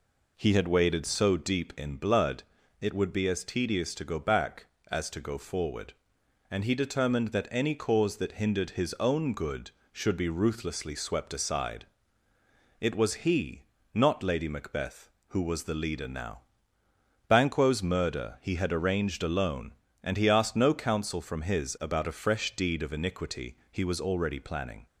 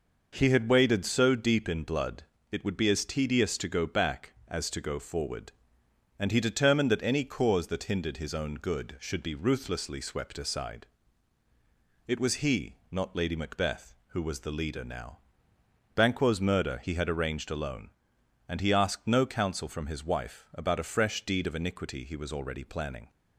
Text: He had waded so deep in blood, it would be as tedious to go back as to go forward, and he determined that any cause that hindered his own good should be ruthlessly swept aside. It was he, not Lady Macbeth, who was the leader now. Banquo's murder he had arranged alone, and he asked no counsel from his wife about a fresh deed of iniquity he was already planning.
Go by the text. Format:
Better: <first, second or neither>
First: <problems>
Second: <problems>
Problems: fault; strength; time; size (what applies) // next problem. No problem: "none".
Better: second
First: skips "wife"; at 21.7 s // pauses between "iniquity" and "he"; slight; at 23.5 s; 0.16 s long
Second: none